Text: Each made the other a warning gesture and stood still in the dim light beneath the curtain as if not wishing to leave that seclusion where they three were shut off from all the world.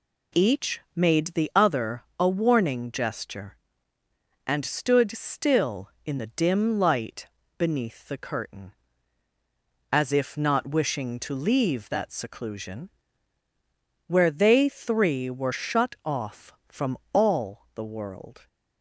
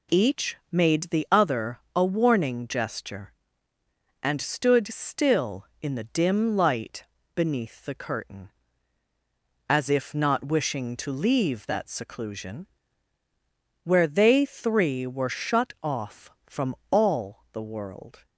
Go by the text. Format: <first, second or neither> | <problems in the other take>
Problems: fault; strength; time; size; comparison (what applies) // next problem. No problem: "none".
neither | pauses between "Each" and "made"; slight; the same in both // pauses between "other" and "a"; slight; the same in both // pauses between "light" and "beneath"; slight; the same in both // pauses between "seclusion" and "where"; the same in both // pauses between "from" and "all"; slight; the same in both